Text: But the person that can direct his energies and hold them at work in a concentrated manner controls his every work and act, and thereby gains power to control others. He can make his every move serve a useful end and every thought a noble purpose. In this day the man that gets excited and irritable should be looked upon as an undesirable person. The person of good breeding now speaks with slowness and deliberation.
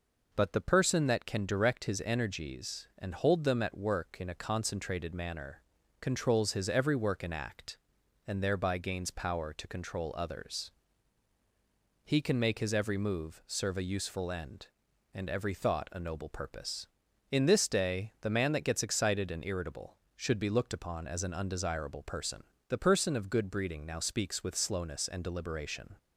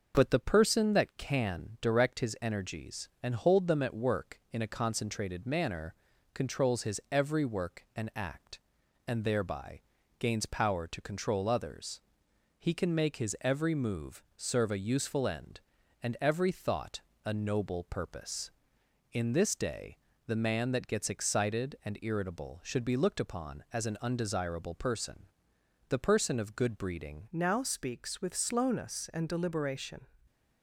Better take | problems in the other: first | pauses between "manner" and "controls"; at 5.9 s; 0.38 s long; slight in the first // pauses between "thereby" and "gains"; slight; at 9.8 s; 0.36 s long // pauses between "move" and "serve"; slight; at 14.2 s; 0.16 s long // pauses between "thought" and "a"; slight; at 17.0 s; 0.24 s long // pauses between "day" and "the"; slight; at 19.9 s; 0.30 s long // changes voice at "now"; from 27.3 s on; 2.7 s long

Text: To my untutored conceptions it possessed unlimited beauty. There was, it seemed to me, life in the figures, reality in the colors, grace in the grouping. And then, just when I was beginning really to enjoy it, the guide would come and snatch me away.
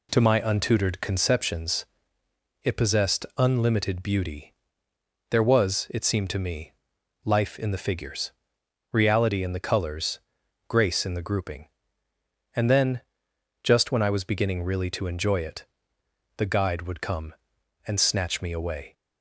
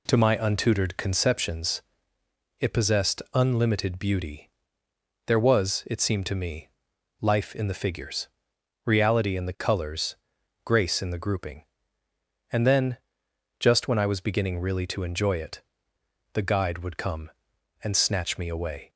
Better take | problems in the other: neither | pauses between "conceptions" and "it"; noticeable; the same in both

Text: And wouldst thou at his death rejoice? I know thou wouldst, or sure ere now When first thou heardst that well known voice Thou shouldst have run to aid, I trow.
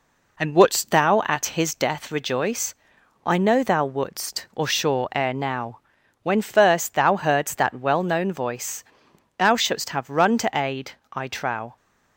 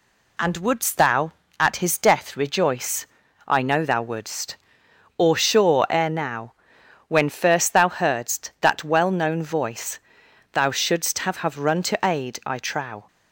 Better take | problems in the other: first | pauses between "now" and "When"; noticeable; at 6.5 s; 0.54 s long; also in the first // pauses between "voice" and "Thou"; noticeable; at 9.9 s; 0.54 s long; noticeable in the first // says "have" twice; at 11.3 s

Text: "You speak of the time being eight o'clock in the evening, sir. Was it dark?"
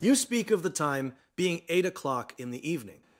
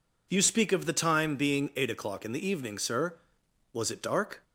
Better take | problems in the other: second | pauses between "time" and "being"; slight; at 1.1 s; 0.22 s long // stops before "sir Was it dark"; at 3.0 s

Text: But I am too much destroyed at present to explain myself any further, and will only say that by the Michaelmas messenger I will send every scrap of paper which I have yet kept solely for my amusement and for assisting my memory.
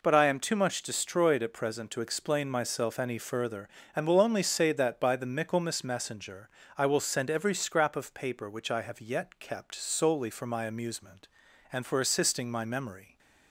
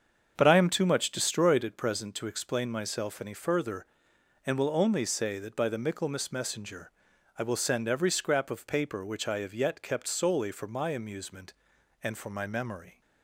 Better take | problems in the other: first | starts louder than the rest; until 1.3 s; 7 dB // pauses between "messenger" and "I"; noticeable; at 6.9 s; 0.48 s long; slight in the first // skips "assisting"; at 12.3 s

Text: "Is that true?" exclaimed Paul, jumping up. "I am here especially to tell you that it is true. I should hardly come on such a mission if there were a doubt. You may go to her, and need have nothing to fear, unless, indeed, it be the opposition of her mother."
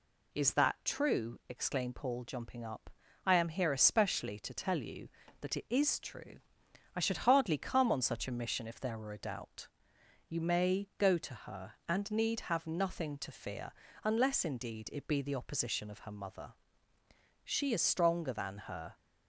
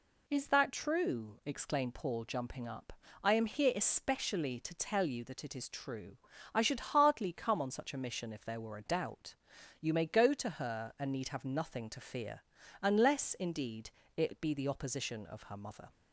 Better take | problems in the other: second | goes on to say "She is stronger than her"; from 17.4 s on; 1.5 s long

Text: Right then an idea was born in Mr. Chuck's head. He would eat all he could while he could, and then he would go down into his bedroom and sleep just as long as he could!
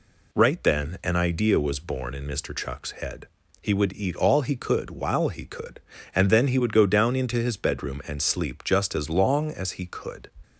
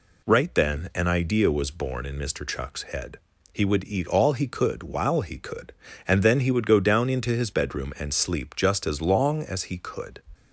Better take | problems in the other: neither | none

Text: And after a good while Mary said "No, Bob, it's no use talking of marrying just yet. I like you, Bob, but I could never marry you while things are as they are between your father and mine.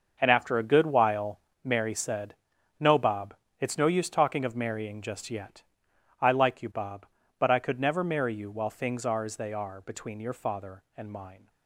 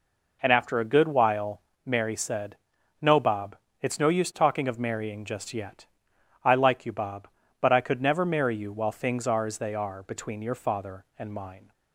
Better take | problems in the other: second | gets quieter; strong; throughout; 12.5 dB // pauses between "while" and "Mary"; slight; at 1.3 s; 0.24 s long; slight in the second // pauses between "said" and "No"; at 2.3 s; 0.44 s long; also in the second

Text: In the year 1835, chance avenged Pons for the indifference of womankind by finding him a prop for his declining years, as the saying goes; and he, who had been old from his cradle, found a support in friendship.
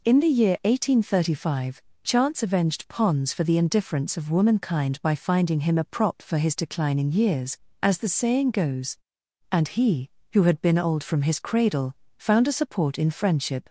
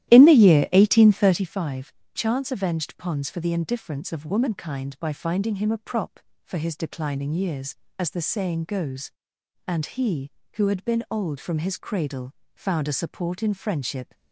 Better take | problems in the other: first | starts louder than the rest; strong; until 1.5 s; 13.5 dB

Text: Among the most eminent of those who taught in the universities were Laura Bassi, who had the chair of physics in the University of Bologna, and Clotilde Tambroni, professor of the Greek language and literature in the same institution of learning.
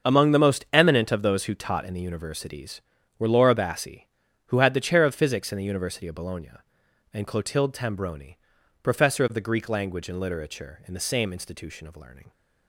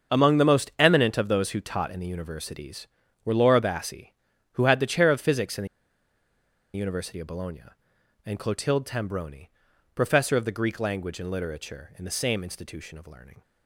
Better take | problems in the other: first | starts louder than the rest; until 1.2 s; 7 dB; also in the first // pauses between "the" and "University"; at 5.6 s; 1.0 s long

